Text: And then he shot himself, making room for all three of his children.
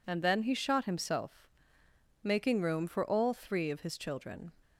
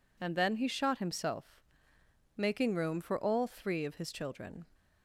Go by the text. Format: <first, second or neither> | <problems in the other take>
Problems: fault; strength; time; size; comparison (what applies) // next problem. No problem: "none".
neither | none